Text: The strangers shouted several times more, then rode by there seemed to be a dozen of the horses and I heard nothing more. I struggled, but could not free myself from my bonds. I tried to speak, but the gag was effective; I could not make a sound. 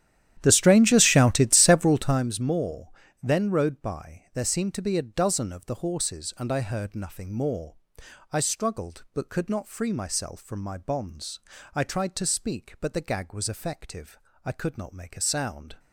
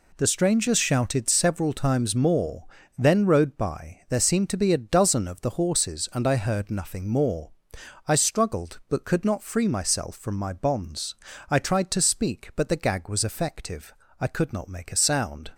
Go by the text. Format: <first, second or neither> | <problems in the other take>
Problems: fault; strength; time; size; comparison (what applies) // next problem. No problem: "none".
second | starts louder than the rest; strong; until 2.3 s; 11.5 dB